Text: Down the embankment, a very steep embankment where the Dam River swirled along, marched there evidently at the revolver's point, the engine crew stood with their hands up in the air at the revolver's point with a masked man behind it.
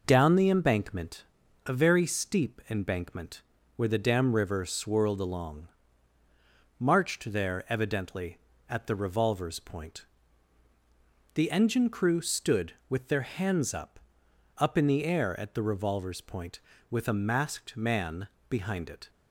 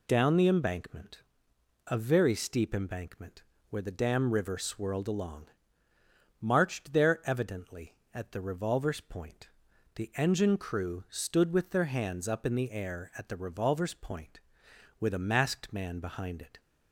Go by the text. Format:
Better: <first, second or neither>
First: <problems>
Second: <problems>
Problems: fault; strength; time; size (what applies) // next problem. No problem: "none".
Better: second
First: pauses between "embankment" and "where"; slight; at 3.4 s; 0.34 s long // says "up" twice; at 14.5 s // pauses between "man" and "behind"; slight; at 18.2 s; 0.20 s long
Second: pauses between "embankment" and "where"; slight; at 3.4 s; 0.26 s long